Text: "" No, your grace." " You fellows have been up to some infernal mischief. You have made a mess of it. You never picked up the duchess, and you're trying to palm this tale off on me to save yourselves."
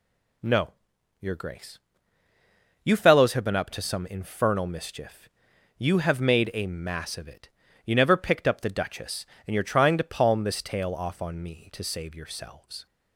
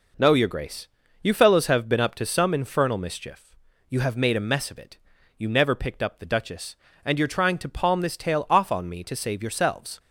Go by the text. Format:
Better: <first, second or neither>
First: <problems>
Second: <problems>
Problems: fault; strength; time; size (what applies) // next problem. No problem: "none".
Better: second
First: says "mass" for "mess"; at 6.6 s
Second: none